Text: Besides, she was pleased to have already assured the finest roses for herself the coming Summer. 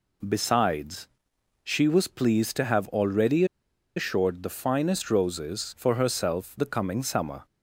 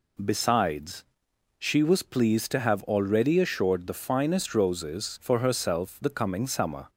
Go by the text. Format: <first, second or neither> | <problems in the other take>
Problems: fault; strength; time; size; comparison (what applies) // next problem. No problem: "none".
second | pauses between "already" and "assured"; noticeable; at 3.4 s; 0.52 s long